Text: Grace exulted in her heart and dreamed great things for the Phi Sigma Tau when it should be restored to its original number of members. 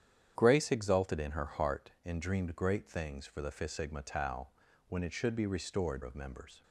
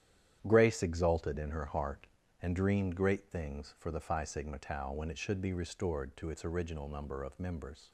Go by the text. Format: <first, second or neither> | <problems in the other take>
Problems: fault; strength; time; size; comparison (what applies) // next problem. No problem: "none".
second | starts louder than the rest; strong; until 1.3 s; 9 dB; strong in the second // pauses between "Tau" and "when"; at 4.4 s; 0.42 s long // skips "to its original number"; at 6.0 s